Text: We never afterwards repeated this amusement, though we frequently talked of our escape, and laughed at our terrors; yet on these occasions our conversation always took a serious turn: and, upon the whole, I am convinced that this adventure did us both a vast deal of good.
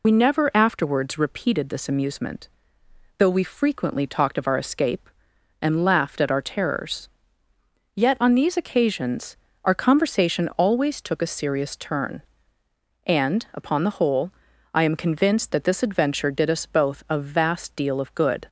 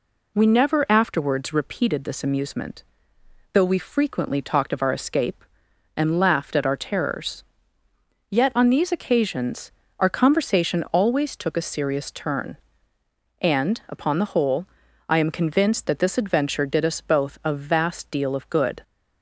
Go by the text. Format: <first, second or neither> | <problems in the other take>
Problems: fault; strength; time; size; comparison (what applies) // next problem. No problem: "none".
second | loses the start of "We"; at 0.0 s; 50 ms // pauses between "occasions" and "our"; slight; at 9.3 s; 0.28 s long; slight in the second